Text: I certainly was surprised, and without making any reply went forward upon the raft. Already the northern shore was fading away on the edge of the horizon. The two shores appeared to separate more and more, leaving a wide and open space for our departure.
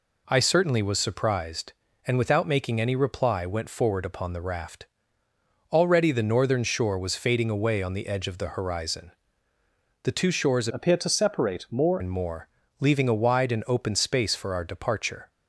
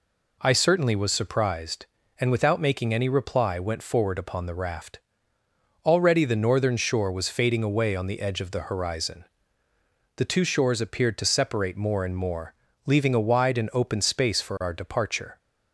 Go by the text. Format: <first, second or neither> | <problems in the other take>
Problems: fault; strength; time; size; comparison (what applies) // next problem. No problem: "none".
second | changes voice from "appeared" to "more"; from 10.7 to 11.9 s; 1.2 s long